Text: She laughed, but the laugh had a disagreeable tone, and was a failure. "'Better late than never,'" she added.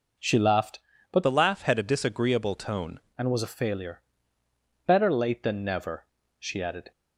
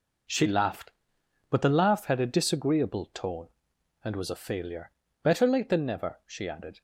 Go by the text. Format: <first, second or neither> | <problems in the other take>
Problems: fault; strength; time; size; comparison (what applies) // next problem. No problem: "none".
second | changes voice from "the" to "tone"; from 1.2 to 2.9 s; 1.7 s long